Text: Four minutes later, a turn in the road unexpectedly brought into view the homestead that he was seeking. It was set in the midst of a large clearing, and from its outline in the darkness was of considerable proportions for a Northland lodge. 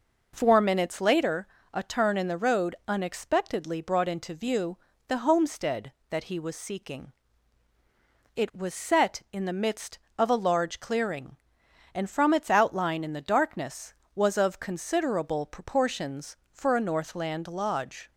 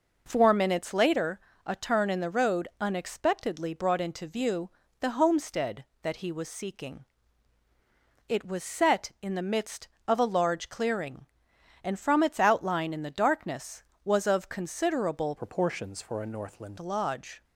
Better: first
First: pauses between "view" and "the"; slight; at 4.7 s; 0.30 s long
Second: pauses between "view" and "the"; slight; at 4.6 s; 0.30 s long // changes voice from "proportions" to "Northland"; from 15.3 to 16.7 s; 1.4 s long

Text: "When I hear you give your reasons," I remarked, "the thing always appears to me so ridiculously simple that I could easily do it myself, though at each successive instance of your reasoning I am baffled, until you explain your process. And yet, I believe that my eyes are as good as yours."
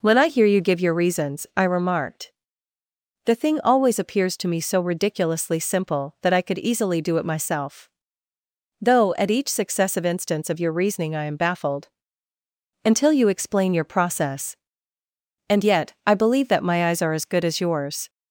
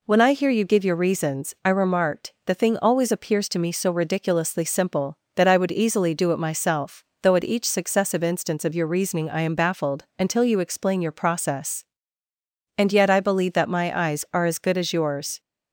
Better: first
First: none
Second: says "would" for "could"; at 5.5 s

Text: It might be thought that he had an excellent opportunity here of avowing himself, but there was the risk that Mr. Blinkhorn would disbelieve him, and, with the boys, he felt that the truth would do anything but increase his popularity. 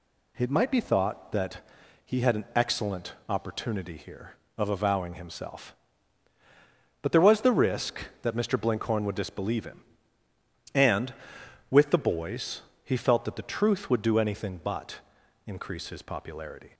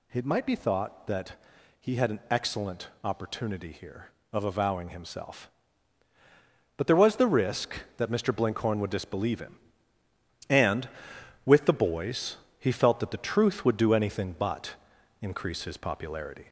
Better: first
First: pauses between "that" and "he"; noticeable; at 1.5 s; 0.46 s long // pauses between "excellent" and "opportunity"; slight; at 3.1 s; 0.16 s long // pauses between "but" and "increase"; noticeable; at 14.9 s; 0.46 s long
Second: gets louder; slight; throughout; 2.5 dB // pauses between "that" and "he"; noticeable; at 1.3 s; 0.46 s long // pauses between "excellent" and "opportunity"; slight; at 2.8 s; 0.16 s long // pauses between "but" and "increase"; noticeable; at 14.7 s; 0.46 s long

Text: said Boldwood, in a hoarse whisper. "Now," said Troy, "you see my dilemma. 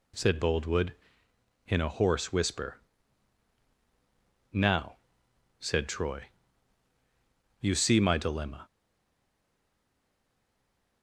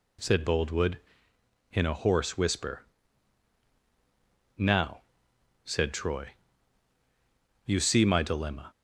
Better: second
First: stays silent after the last word; from 8.6 s on; 2.4 s long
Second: none

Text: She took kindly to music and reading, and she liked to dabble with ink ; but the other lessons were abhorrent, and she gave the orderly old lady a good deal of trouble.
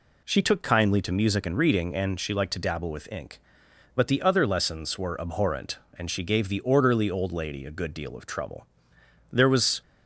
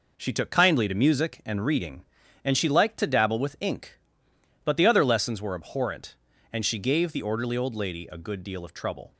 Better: second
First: goes on to say "There was"; slight; from 9.3 s on; 0.48 s long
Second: none

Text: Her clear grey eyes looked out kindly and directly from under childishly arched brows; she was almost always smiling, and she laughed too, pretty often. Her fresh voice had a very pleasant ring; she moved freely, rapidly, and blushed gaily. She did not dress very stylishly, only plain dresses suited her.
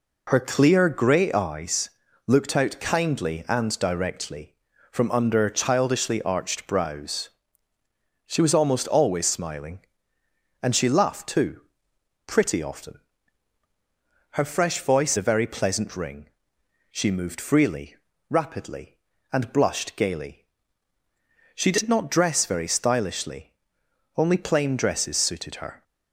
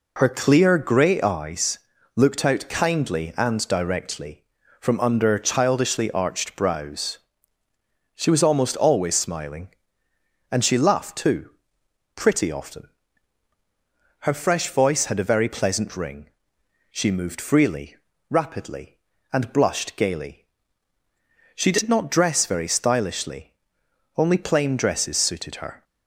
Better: second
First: pauses between "eyes" and "looked"; at 1.8 s; 0.38 s long // skips "had"; at 15.1 s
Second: pauses between "eyes" and "looked"; at 1.7 s; 0.38 s long

